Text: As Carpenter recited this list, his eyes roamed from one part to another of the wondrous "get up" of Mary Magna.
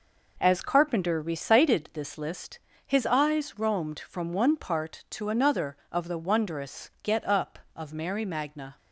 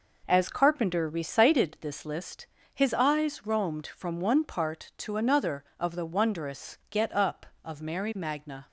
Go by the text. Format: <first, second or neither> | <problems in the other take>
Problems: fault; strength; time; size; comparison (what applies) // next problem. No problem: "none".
neither | none